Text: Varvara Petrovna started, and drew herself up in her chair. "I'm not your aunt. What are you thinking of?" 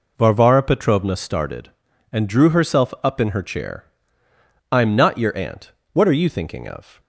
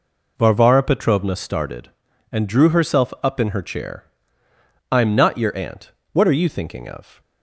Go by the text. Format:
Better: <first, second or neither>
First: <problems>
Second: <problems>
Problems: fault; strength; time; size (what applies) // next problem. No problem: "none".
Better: neither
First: none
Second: none